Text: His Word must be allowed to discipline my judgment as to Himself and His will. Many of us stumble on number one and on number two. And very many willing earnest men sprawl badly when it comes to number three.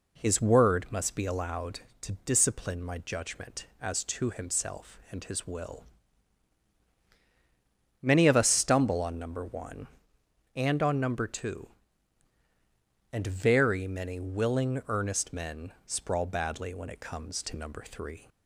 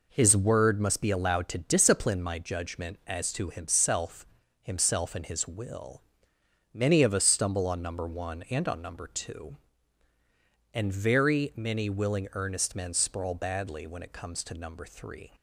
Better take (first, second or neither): first